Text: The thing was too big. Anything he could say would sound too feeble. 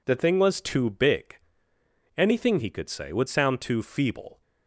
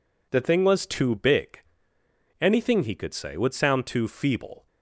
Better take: neither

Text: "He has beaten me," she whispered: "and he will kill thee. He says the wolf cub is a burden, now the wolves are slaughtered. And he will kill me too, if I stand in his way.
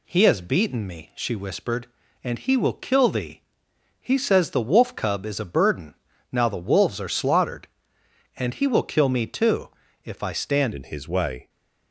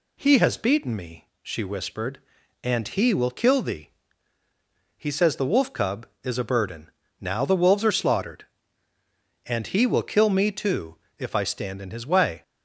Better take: second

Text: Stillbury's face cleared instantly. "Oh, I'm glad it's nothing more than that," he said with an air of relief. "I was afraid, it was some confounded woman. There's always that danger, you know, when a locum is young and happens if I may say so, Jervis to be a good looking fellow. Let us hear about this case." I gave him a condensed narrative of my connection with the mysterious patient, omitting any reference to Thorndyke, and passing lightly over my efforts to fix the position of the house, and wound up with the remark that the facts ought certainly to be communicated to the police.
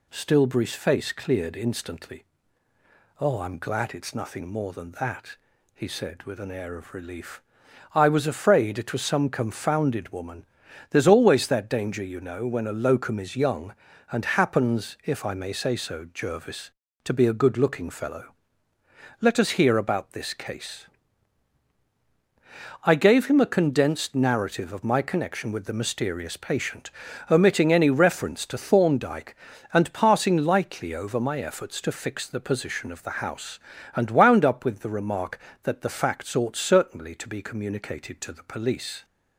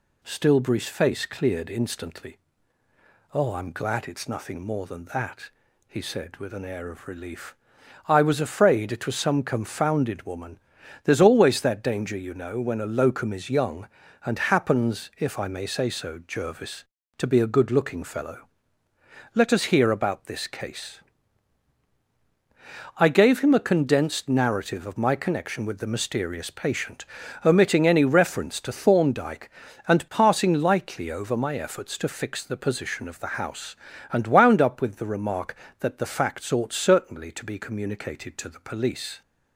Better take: neither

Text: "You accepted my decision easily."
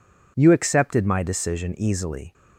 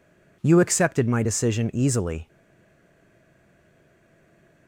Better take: first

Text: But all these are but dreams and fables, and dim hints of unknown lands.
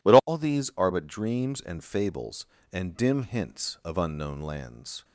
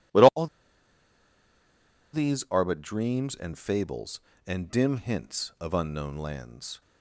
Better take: first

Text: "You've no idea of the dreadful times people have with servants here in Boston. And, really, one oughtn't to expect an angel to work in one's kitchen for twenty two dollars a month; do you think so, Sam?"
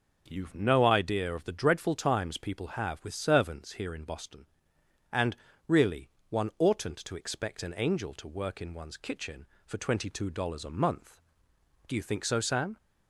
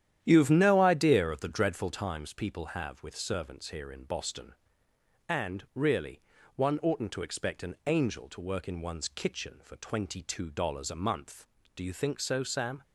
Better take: first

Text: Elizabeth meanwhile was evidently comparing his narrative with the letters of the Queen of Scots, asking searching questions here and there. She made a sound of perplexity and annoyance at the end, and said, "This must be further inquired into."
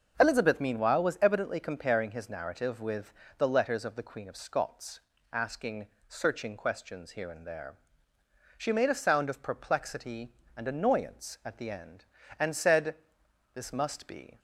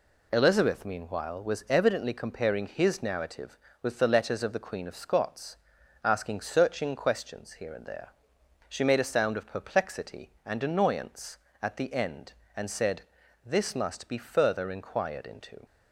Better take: second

